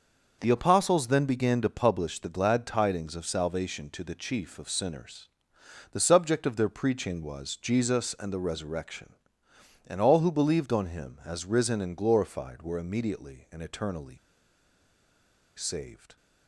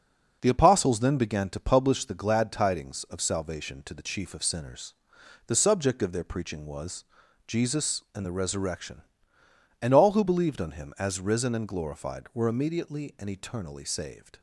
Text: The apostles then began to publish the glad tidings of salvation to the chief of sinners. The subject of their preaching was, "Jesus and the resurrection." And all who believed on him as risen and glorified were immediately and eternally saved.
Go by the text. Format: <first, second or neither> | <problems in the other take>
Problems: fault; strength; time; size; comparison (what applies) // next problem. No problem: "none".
second | starts louder than the rest; until 1.4 s; 6 dB; noticeable in the second // pauses between "eternally" and "saved"; strong; at 14.1 s; 1.4 s long